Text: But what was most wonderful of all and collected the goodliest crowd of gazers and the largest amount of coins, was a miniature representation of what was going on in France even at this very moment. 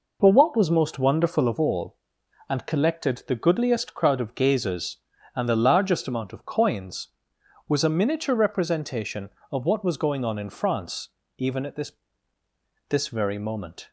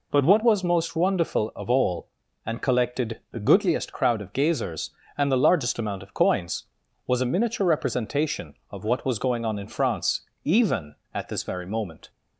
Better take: second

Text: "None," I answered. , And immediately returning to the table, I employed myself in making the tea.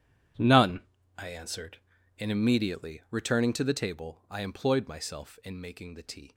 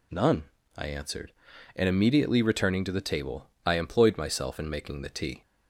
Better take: second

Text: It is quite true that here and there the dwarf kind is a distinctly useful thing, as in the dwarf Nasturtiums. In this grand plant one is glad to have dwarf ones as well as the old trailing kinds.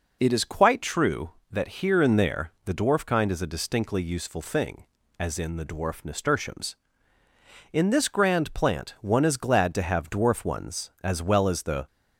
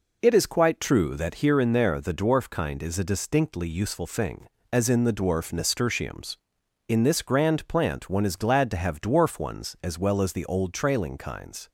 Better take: second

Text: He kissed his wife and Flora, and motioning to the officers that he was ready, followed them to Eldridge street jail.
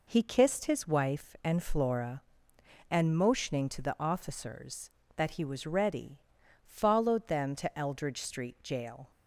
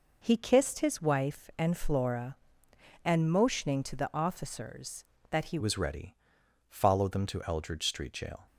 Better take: first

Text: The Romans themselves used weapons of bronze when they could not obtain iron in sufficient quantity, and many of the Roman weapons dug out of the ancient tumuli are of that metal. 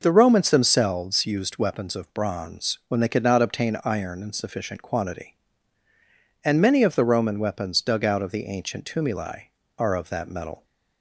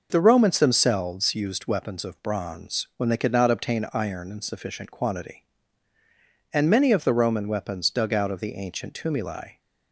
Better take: first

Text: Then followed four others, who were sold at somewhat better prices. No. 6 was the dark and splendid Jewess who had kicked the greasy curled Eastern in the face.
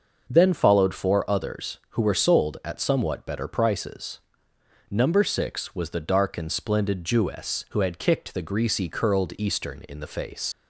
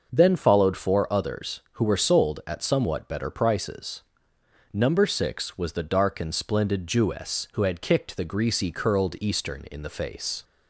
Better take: second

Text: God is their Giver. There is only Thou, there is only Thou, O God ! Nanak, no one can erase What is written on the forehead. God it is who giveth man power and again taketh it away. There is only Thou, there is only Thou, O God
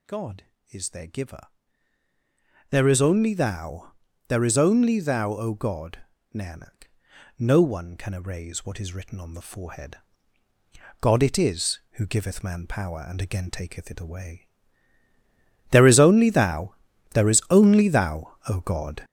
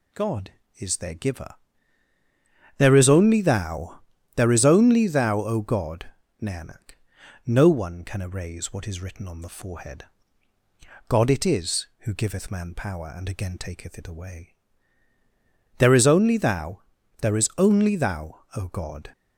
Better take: second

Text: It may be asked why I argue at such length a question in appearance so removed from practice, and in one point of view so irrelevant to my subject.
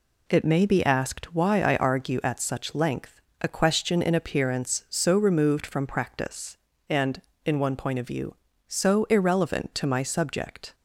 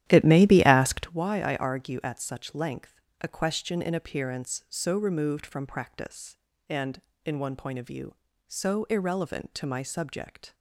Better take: first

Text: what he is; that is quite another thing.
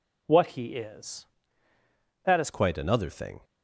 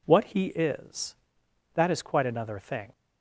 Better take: second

